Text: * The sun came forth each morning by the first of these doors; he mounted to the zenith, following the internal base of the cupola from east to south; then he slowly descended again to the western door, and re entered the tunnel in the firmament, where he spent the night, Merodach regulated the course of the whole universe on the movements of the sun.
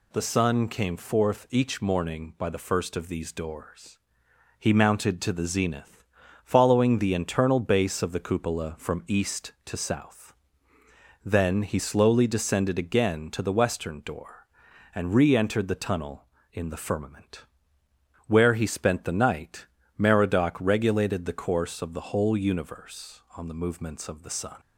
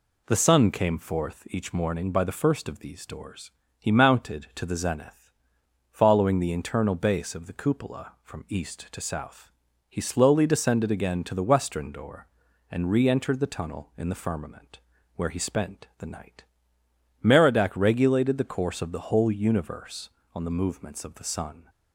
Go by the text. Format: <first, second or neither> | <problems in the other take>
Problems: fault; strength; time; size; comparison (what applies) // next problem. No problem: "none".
first | skips "then"; at 9.6 s